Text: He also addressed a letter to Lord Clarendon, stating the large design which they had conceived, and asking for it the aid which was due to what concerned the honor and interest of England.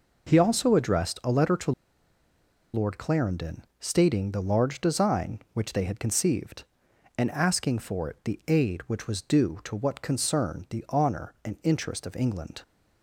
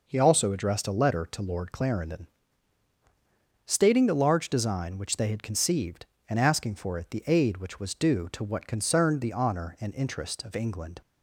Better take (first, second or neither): second